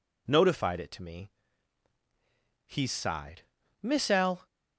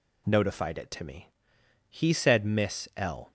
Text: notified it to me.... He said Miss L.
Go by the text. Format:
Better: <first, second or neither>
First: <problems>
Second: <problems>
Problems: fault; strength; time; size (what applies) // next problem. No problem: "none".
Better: second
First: says "sighed" for "said"; at 2.8 s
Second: none